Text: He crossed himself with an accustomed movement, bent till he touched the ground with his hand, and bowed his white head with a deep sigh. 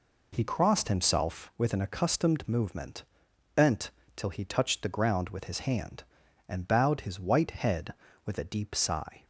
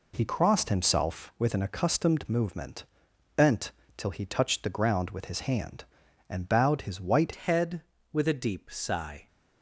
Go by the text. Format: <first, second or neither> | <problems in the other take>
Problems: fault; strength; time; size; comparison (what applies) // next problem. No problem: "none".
first | pauses between "bent" and "till"; slight; at 3.7 s; 0.24 s long; slight in the first // changes voice at "head"; from 7.3 s on; 1.9 s long